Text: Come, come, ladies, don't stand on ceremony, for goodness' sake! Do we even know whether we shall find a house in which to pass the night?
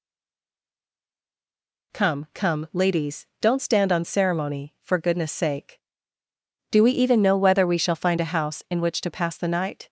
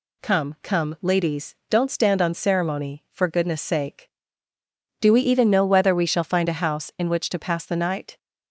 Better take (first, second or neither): second